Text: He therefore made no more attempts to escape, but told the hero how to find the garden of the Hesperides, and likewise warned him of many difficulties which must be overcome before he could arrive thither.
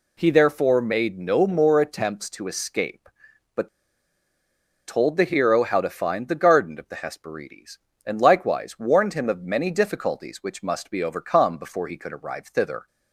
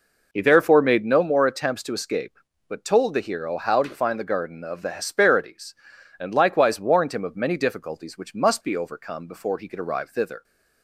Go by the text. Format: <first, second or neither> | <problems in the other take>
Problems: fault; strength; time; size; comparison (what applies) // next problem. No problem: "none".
second | pauses between "but" and "told"; at 3.6 s; 1.1 s long